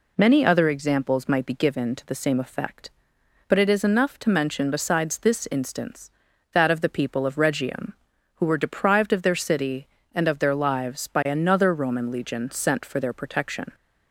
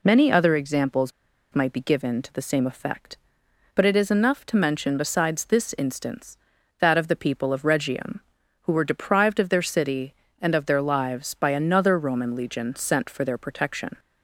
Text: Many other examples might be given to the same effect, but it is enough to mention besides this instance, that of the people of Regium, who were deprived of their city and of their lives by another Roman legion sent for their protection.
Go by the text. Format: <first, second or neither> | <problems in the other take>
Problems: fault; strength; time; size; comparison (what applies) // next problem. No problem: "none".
first | pauses between "examples" and "might"; at 1.1 s; 0.42 s long